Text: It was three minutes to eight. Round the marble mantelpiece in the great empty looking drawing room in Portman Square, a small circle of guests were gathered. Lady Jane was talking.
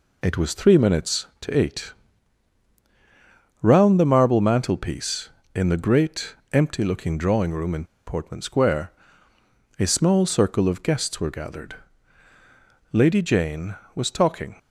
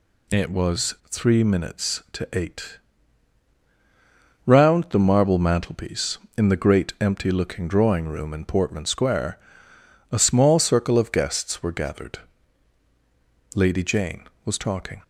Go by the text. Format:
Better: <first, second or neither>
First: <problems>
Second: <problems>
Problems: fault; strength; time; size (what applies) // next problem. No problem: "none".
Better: second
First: pauses between "great" and "empty"; slight; at 6.3 s; 0.18 s long // pauses between "in" and "Portman"; slight; at 7.8 s; 0.21 s long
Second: none